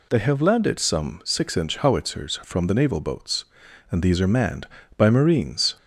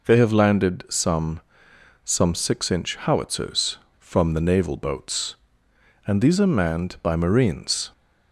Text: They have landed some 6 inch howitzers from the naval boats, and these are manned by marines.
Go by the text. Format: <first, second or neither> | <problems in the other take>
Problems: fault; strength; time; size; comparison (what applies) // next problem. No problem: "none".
first | says "some" twice; at 2.0 s